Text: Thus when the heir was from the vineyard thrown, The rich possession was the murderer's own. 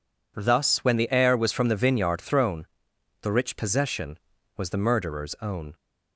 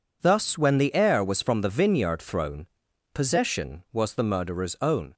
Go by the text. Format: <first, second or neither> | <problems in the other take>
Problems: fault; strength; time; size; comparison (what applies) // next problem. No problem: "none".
first | skips "The rich"; at 2.8 s